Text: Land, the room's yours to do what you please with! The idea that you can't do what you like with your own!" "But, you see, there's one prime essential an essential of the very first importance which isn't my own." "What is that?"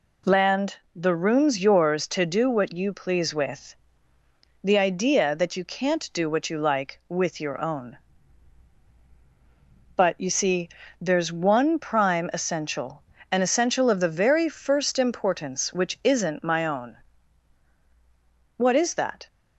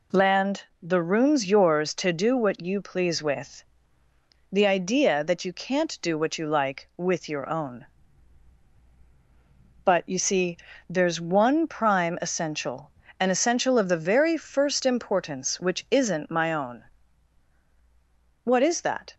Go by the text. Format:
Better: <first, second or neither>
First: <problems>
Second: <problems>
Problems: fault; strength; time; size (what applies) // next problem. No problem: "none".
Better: neither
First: pauses between "essential" and "an"; slight; at 13.0 s; 0.30 s long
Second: pauses between "essential" and "an"; slight; at 12.9 s; 0.30 s long